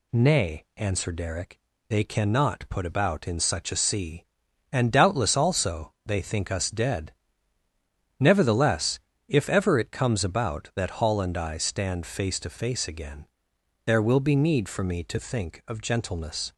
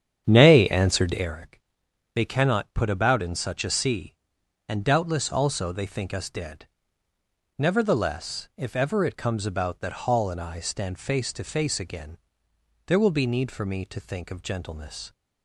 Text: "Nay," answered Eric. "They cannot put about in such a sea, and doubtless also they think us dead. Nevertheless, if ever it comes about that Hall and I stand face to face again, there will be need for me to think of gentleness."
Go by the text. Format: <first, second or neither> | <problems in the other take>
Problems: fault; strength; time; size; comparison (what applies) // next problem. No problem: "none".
first | starts louder than the rest; strong; until 1.3 s; 8.5 dB